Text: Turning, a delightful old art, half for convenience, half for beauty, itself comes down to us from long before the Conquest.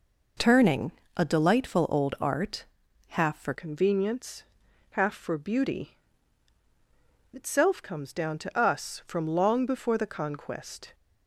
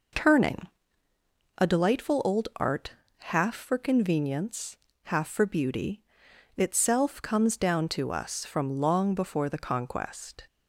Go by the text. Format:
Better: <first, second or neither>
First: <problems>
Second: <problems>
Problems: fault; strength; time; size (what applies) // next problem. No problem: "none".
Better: second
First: changes voice at "convenience"; from 3.5 s on; 7.4 s long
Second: none